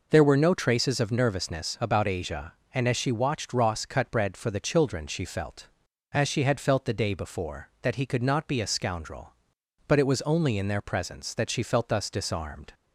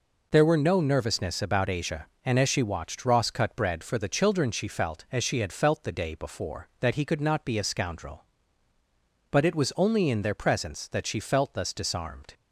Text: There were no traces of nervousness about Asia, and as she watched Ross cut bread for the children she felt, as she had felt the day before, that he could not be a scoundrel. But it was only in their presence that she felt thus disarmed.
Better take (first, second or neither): first